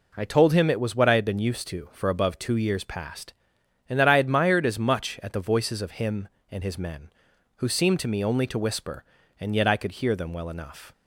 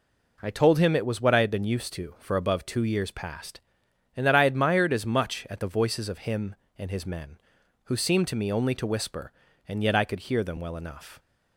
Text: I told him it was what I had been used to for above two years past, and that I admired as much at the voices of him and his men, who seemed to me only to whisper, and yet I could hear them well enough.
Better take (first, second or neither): neither